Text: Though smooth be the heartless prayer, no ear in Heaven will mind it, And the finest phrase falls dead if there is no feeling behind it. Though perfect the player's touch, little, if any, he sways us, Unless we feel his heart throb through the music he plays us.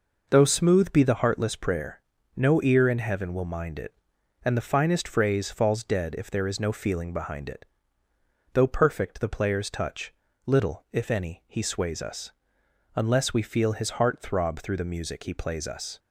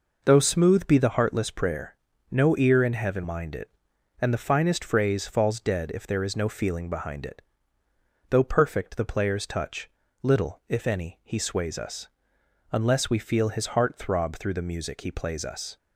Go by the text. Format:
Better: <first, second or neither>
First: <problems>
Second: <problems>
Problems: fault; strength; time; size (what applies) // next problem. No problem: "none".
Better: first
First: none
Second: skips "will"; at 3.2 s